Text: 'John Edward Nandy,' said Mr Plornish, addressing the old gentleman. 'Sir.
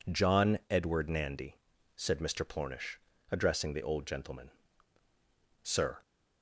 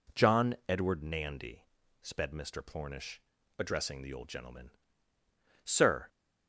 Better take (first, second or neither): first